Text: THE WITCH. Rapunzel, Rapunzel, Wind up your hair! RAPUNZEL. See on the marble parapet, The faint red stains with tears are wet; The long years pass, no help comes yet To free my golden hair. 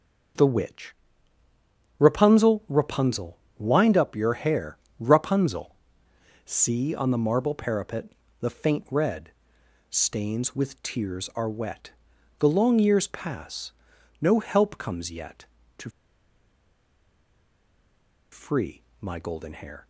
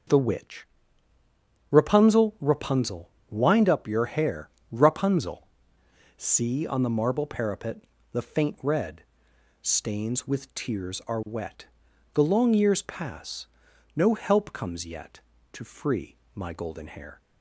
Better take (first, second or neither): second